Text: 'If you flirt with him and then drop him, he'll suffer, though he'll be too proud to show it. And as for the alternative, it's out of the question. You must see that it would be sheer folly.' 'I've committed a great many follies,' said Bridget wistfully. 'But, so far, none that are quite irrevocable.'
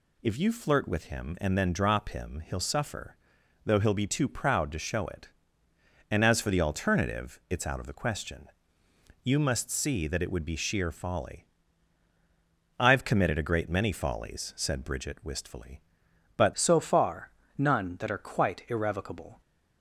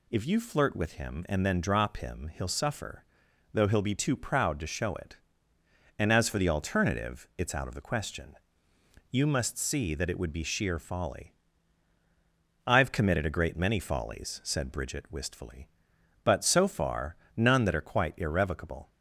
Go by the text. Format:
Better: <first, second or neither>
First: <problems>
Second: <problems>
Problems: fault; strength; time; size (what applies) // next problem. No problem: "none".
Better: second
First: changes voice at "so"; from 16.5 s on; 2.9 s long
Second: none